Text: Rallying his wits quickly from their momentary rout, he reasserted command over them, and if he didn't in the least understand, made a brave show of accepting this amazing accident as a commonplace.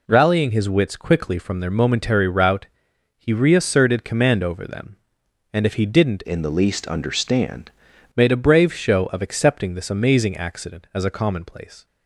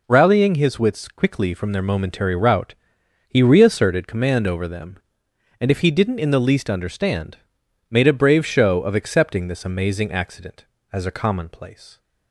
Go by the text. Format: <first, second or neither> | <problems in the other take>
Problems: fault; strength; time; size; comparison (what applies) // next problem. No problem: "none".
second | changes voice from "in" to "understand"; from 6.2 to 7.6 s; 1.4 s long